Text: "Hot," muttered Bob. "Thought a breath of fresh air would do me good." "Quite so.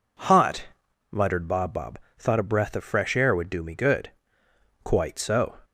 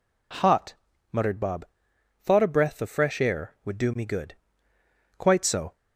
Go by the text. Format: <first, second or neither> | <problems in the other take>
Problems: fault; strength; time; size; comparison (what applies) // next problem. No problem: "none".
second | says "Bob" twice; at 1.7 s